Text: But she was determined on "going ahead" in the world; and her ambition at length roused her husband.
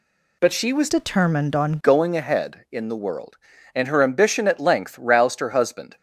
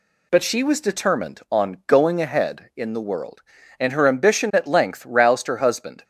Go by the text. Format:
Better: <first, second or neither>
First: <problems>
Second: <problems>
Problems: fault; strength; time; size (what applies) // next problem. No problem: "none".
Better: second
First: changes voice from "determined" to "on"; from 0.8 to 1.7 s; 0.9 s long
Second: none